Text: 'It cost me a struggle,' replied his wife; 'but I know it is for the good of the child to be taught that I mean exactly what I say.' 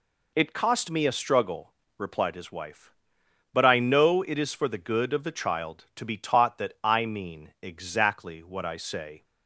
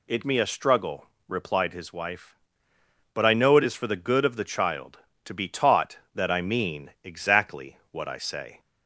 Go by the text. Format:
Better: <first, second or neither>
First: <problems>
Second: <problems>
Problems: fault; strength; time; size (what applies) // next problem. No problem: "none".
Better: first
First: none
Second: skips "cost"; at 0.2 s